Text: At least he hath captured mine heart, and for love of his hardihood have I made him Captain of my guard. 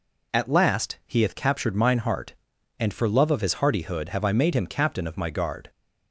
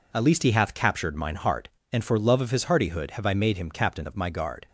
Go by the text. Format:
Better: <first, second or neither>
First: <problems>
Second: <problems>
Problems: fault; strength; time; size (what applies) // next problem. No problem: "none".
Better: second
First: says "last" for "least"; at 0.4 s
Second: none